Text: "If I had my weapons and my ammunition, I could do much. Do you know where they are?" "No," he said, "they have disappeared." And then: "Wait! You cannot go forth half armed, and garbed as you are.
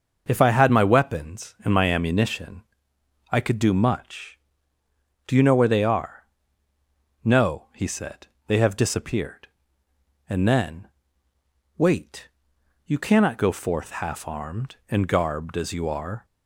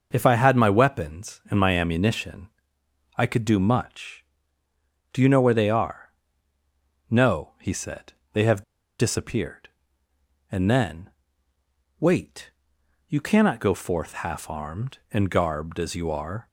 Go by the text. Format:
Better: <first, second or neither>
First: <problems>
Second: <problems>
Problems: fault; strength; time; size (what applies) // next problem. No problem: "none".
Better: first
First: none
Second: pauses between "have" and "disappeared"; at 8.6 s; 0.37 s long